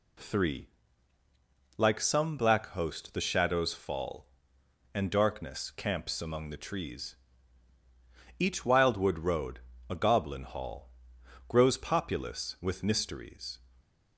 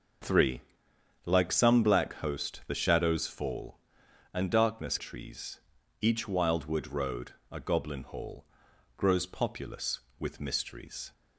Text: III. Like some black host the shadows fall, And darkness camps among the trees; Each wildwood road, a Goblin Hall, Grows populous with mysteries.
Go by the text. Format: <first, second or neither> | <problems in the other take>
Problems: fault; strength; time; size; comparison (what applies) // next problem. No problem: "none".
first | skips "camps among the"; at 4.9 s